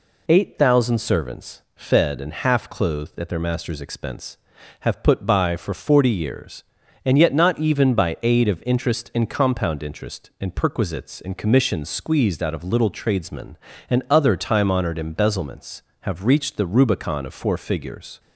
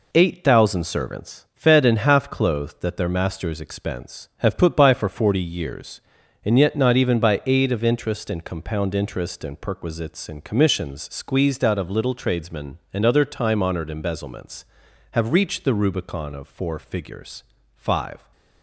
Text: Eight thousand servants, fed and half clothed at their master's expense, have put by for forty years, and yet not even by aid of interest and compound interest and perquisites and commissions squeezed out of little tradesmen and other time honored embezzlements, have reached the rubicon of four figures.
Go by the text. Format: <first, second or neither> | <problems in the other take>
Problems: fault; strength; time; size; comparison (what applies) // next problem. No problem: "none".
first | goes on to say "Five"; from 17.7 s on; 0.54 s long